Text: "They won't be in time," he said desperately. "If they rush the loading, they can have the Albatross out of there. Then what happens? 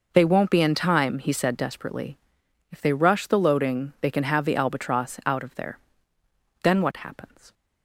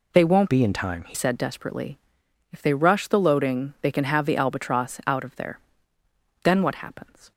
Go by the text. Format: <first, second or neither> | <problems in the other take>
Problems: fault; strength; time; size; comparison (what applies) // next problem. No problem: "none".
first | changes voice from "be" to "he"; from 0.4 to 1.1 s; 0.7 s long